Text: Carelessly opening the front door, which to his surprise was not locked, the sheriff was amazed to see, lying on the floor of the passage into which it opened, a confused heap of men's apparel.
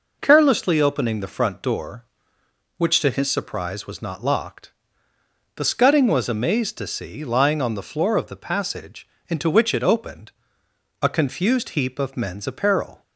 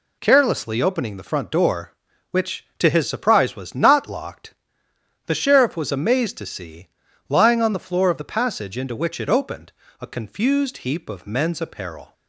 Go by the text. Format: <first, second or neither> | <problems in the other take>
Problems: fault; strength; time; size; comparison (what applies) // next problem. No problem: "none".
second | says "scudding" for "sheriff"; at 5.6 s // pauses between "passage" and "into"; slight; at 9.0 s; 0.22 s long